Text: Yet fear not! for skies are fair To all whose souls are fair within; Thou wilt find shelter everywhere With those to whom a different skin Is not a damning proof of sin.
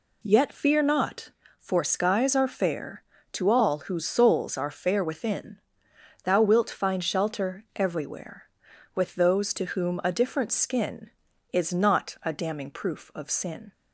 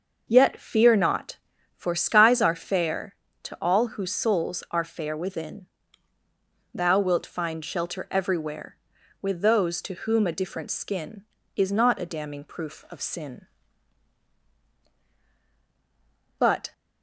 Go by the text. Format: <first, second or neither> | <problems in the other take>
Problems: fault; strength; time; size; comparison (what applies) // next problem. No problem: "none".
first | starts louder than the rest; noticeable; until 1.2 s; 6 dB // goes on to say "But"; slight; from 16.3 s on; 0.34 s long